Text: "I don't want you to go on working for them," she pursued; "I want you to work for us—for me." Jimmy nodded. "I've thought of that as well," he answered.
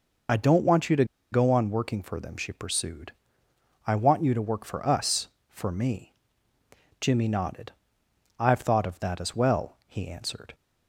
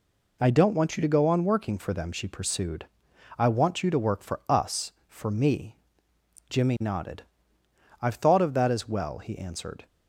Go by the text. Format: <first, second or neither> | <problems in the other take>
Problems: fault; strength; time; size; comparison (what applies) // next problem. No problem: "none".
second | pauses between "to" and "go"; slight; at 1.0 s; 0.27 s long